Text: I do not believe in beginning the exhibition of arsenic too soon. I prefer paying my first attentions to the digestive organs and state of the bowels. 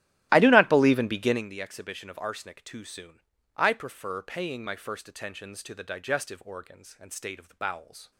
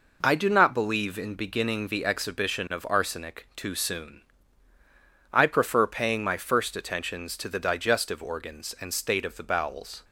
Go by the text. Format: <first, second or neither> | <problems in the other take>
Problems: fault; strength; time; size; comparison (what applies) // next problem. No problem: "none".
second | starts louder than the rest; strong; until 1.5 s; 15 dB